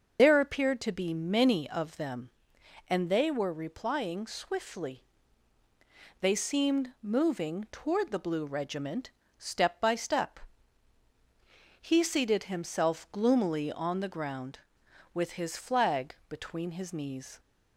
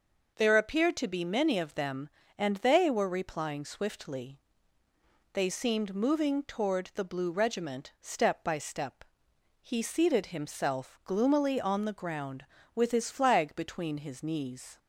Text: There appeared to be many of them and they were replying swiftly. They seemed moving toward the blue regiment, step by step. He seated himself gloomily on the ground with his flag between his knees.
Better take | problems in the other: second | loses the start of "There"; at 0.1 s; 100 ms // starts louder than the rest; until 1.2 s; 6.5 dB

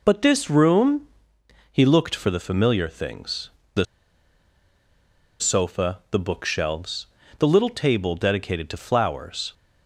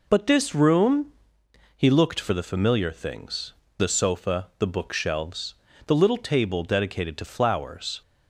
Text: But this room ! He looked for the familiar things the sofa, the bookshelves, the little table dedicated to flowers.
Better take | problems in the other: second | pauses between "things" and "the"; slight; at 3.5 s; 0.24 s long; slight in the second // pauses between "the" and "sofa"; strong; at 3.8 s; 1.5 s long

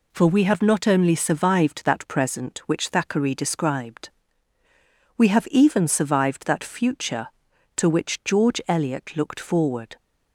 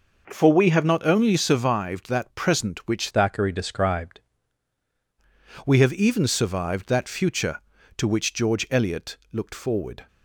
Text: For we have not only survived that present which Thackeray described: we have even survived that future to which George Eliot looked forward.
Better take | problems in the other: first | changes voice from "Thackeray" to "described"; from 3.0 to 4.1 s; 1.1 s long

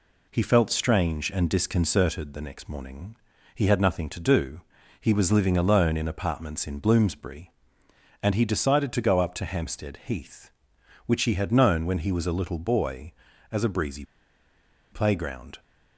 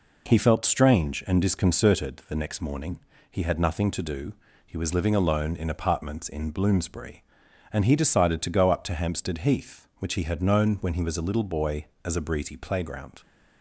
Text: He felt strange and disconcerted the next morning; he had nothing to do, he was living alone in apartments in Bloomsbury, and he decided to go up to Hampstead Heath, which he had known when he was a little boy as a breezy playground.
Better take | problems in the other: second | pauses between "breezy" and "playground"; noticeable; at 14.0 s; 0.87 s long

